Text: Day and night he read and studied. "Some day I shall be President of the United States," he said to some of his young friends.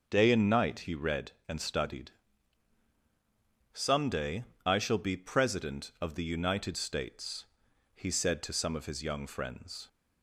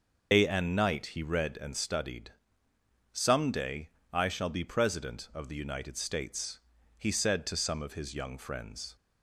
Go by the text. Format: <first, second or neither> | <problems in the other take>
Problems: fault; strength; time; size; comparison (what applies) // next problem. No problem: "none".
first | loses the start of "Day"; at 0.3 s; 105 ms // starts louder than the rest; noticeable; until 1.3 s; 6 dB; noticeable in the first // pauses between "day" and "I"; slight; at 3.8 s; 0.24 s long; slight in the first